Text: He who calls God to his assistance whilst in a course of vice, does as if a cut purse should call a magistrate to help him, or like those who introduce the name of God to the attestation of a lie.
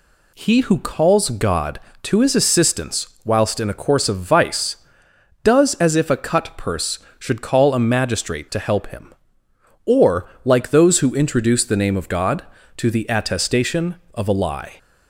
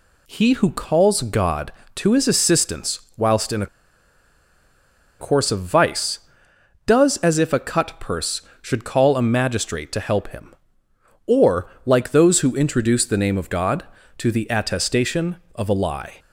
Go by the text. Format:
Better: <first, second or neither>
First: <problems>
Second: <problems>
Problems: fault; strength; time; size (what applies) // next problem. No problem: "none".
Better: first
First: pauses between "assistance" and "whilst"; slight; at 3.0 s; 0.16 s long // pauses between "or" and "like"; slight; at 10.2 s; 0.16 s long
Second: pauses between "assistance" and "whilst"; slight; at 3.0 s; 0.16 s long // pauses between "a" and "course"; strong; at 3.6 s; 1.5 s long // pauses between "or" and "like"; slight; at 11.6 s; 0.16 s long